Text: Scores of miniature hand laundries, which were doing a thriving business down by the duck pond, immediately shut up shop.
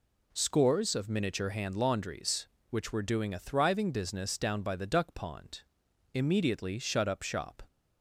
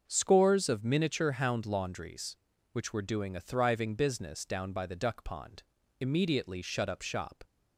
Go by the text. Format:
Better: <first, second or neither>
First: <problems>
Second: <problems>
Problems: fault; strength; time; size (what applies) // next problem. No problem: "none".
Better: first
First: none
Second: starts louder than the rest; until 1.0 s; 6.5 dB // says "hound" for "hand"; at 1.3 s